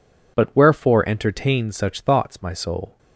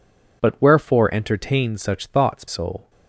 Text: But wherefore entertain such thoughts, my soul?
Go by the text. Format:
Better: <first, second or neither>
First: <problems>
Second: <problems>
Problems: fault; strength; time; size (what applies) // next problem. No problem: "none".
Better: first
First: none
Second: skips "my"; at 2.4 s